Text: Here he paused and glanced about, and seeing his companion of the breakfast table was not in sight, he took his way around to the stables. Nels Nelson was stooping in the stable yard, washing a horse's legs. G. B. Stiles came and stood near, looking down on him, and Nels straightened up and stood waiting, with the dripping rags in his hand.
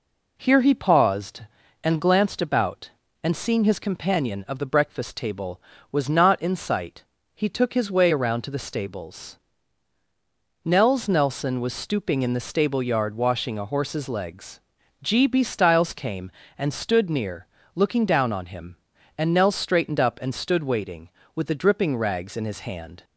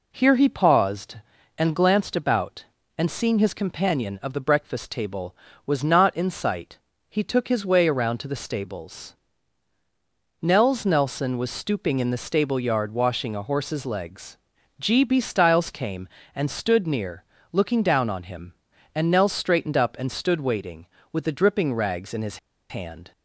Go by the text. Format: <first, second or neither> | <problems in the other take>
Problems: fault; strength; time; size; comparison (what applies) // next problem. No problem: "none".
first | pauses between "his" and "hand"; slight; at 22.3 s; 0.32 s long